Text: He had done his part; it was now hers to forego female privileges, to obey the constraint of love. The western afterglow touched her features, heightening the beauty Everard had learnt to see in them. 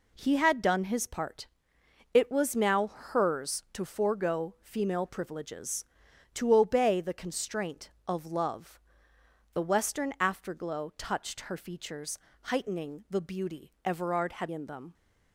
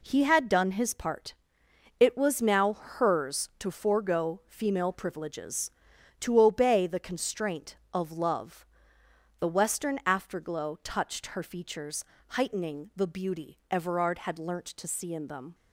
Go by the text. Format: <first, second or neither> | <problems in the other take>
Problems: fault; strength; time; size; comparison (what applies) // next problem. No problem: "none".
second | skips "learnt to see"; at 14.5 s